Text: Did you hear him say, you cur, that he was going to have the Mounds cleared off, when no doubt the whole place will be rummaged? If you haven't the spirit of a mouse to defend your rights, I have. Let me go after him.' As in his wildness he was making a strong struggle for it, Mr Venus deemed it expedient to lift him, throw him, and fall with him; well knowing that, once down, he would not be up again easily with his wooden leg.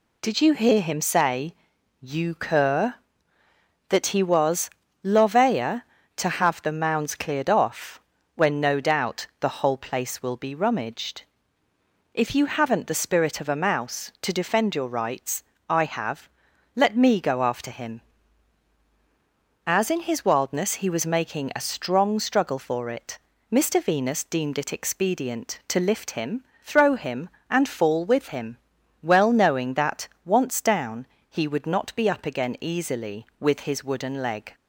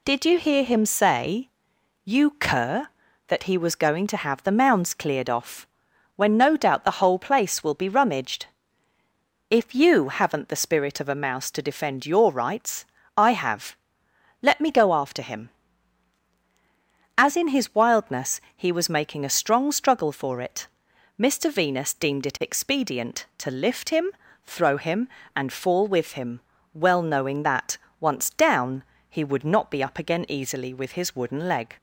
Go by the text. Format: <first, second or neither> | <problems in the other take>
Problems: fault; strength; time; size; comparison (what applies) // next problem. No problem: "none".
second | says "lovea" for "going"; at 5.0 s